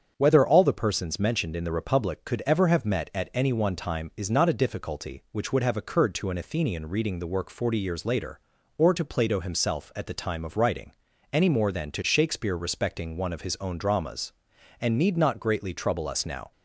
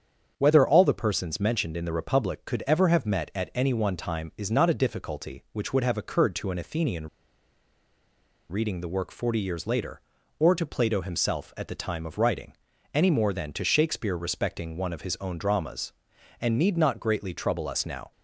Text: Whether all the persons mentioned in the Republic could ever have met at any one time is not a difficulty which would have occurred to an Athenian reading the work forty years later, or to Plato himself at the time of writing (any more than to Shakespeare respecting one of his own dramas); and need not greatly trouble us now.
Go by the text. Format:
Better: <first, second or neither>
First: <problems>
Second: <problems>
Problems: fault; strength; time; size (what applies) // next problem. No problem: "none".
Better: first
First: starts louder than the rest; strong; until 1.1 s; 7.5 dB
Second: starts louder than the rest; strong; until 1.3 s; 7 dB // pauses between "Athenian" and "reading"; strong; at 7.0 s; 1.4 s long